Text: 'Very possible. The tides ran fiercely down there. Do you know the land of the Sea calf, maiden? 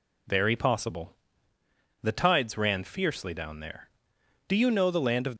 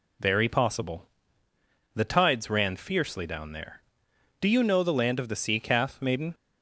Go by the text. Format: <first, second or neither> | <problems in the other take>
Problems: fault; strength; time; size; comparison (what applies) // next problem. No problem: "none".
second | stops before "the Sea calf maiden"; at 5.3 s